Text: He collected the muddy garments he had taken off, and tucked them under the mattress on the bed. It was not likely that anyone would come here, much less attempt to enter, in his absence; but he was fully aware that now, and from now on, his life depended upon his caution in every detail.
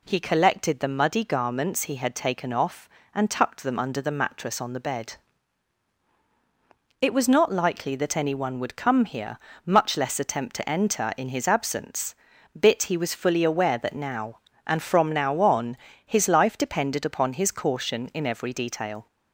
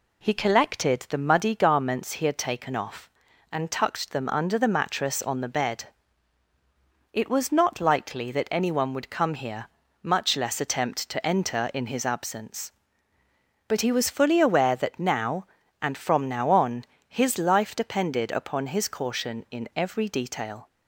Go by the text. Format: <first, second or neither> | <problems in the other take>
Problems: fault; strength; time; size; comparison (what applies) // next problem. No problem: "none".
second | says "bit" for "but"; at 12.5 s